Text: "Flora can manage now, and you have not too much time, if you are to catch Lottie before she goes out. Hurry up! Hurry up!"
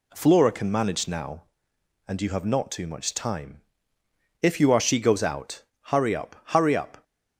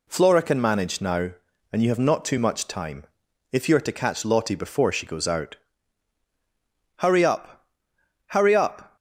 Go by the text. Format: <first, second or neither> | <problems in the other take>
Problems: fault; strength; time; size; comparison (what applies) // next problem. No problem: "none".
second | skips "to catch Lottie before"; at 4.8 s